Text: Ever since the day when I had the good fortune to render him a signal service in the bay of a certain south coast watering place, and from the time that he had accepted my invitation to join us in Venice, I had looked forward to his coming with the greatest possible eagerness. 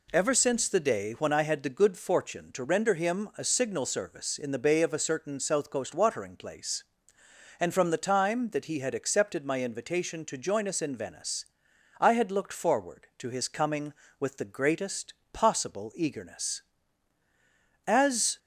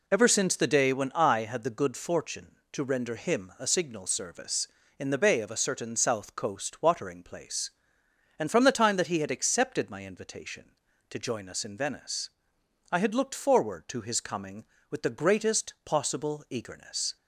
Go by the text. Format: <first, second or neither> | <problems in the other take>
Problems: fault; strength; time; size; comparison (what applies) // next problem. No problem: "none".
second | pauses between "greatest" and "possible"; slight; at 15.1 s; 0.18 s long // goes on to say "As"; from 17.8 s on; 0.54 s long